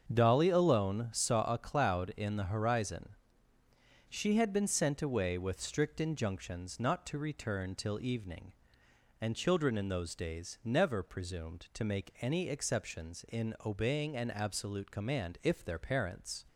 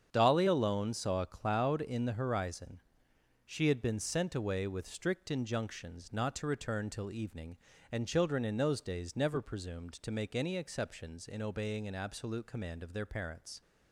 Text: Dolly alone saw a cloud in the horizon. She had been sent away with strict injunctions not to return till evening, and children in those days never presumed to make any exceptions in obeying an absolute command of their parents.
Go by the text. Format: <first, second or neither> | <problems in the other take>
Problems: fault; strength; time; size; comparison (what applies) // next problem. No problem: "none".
second | starts louder than the rest; until 1.1 s; 7 dB; strong in the second // says "if" for "of"; at 15.4 s